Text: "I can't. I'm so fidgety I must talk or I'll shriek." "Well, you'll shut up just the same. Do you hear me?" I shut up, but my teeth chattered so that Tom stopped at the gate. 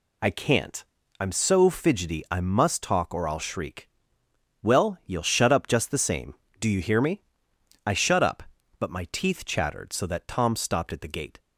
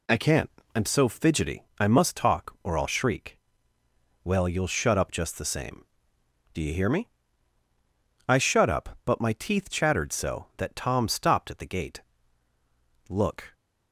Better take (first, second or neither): first